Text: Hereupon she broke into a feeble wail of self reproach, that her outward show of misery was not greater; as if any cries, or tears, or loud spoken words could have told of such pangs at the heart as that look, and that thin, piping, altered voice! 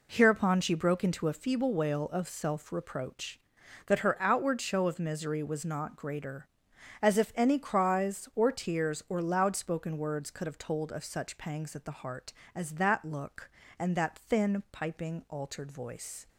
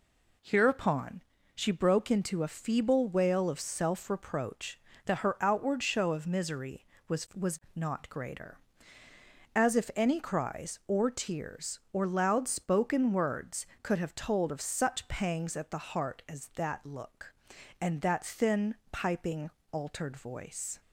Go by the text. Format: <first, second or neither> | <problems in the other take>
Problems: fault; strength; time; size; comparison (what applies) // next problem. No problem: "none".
first | pauses between "Hereupon" and "she"; slight; at 1.2 s; 0.34 s long // says "was" twice; at 7.3 s